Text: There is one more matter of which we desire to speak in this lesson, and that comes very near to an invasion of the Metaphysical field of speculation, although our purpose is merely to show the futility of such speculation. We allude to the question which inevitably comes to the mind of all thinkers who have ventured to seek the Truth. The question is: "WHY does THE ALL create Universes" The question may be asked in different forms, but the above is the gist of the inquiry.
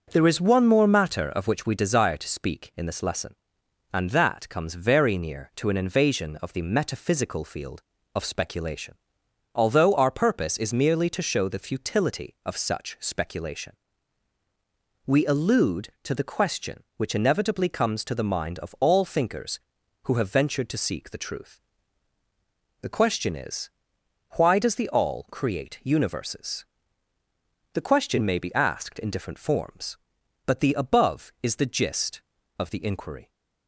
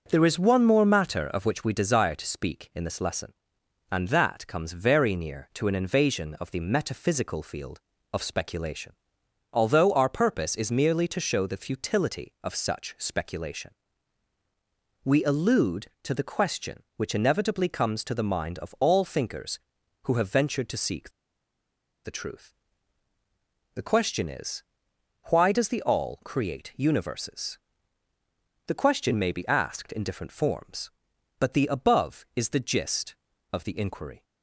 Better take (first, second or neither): first